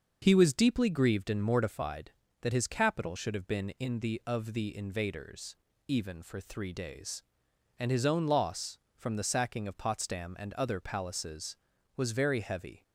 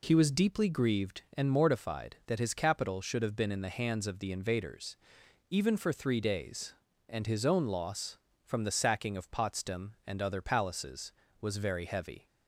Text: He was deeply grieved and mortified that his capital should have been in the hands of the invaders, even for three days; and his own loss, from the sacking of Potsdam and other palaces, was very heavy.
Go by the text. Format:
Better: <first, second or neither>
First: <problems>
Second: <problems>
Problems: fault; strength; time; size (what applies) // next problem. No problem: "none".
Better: second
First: starts louder than the rest; until 1.2 s; 6 dB // skips "hands"; at 4.2 s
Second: none